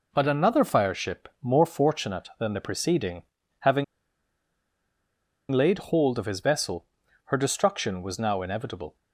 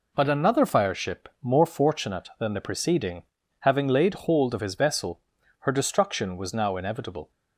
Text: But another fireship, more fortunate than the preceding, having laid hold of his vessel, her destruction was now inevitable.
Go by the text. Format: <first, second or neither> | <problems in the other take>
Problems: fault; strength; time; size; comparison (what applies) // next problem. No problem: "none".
second | pauses between "having" and "laid"; strong; at 3.8 s; 1.6 s long